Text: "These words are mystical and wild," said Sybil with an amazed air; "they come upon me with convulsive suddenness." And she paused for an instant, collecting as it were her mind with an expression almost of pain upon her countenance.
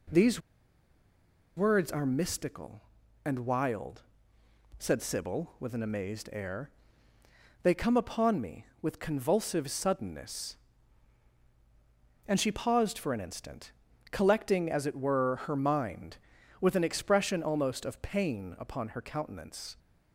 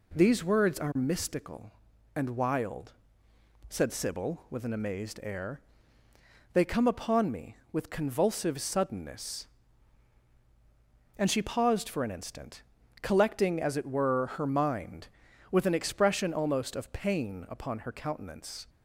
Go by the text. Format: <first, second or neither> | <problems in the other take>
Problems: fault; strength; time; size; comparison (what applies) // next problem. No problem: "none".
second | pauses between "These" and "words"; at 0.4 s; 1.1 s long